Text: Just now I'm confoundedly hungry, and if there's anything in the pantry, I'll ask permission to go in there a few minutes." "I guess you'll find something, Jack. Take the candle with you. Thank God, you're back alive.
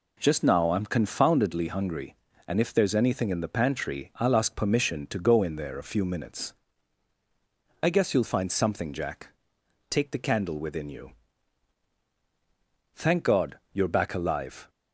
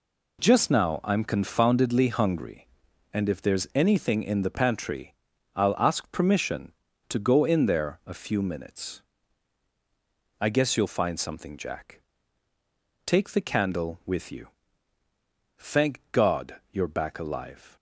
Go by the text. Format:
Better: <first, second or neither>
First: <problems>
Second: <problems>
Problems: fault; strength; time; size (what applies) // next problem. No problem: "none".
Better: second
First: says "within" for "with"; at 10.5 s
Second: none